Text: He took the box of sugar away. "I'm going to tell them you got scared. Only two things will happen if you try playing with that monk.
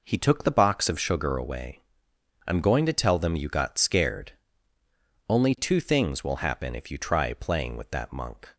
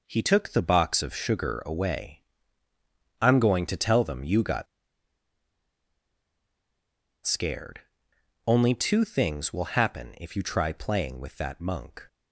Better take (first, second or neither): first